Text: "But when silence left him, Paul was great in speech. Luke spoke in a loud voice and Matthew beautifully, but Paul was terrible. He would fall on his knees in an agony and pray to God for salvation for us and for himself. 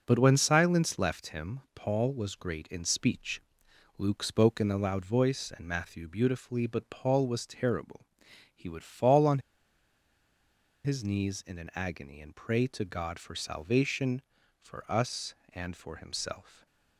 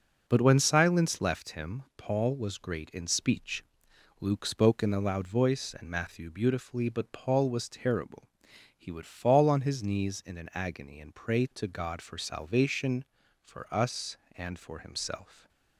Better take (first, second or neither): second